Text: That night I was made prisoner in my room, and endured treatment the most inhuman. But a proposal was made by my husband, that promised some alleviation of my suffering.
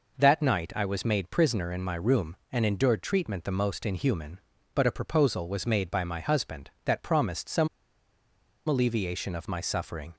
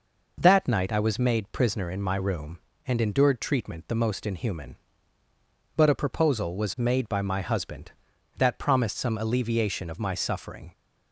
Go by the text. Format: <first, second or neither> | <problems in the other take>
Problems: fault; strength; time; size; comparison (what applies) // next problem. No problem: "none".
second | pauses between "some" and "alleviation"; at 7.6 s; 0.98 s long